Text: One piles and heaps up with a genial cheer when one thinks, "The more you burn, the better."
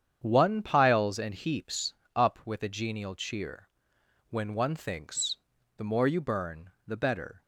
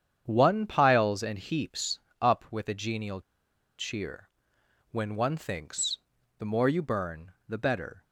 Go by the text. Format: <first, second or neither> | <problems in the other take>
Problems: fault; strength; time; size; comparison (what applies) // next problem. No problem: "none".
first | starts louder than the rest; strong; until 1.2 s; 8.5 dB; strong in the first // pauses between "heaps" and "up"; slight; at 2.0 s; 0.20 s long; slight in the first // pauses between "genial" and "cheer"; noticeable; at 3.2 s; 0.57 s long // pauses between "cheer" and "when"; noticeable; at 4.2 s; 0.60 s long; noticeable in the first